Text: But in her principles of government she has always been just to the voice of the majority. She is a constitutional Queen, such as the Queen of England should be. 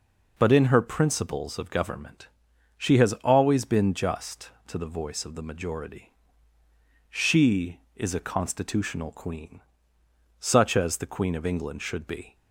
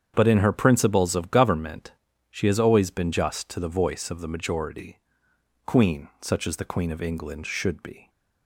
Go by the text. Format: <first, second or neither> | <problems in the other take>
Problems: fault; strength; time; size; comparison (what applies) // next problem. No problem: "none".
first | starts louder than the rest; strong; until 1.1 s; 7.5 dB // pauses between "government" and "she"; at 1.9 s; 0.40 s long; noticeable in the first // skips "She is a constitutional"; at 5.3 s